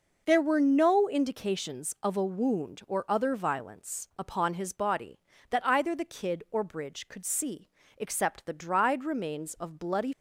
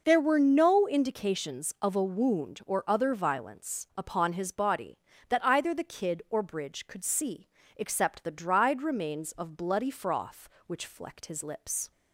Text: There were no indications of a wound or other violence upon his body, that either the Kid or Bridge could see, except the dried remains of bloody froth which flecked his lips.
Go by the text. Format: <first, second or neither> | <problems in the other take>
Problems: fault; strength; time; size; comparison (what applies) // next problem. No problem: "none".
second | stops before "froth which flecked his lips"; at 10.1 s